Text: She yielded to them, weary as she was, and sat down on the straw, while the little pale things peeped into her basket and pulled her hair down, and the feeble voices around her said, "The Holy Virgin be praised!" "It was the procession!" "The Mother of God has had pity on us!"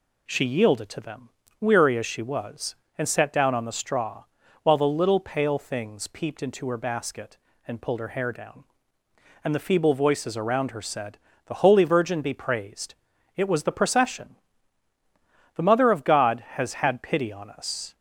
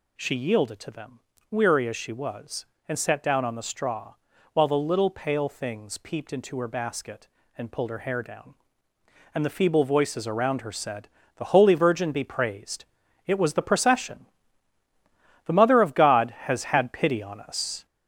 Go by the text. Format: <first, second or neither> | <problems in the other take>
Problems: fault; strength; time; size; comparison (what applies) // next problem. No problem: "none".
first | gets louder; noticeable; throughout; 4.5 dB